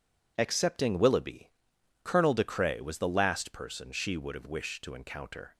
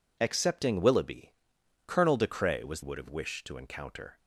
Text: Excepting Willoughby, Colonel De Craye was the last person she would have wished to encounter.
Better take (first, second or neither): first